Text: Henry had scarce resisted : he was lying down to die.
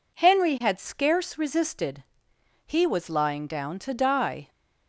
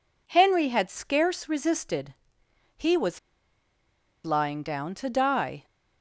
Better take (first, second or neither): first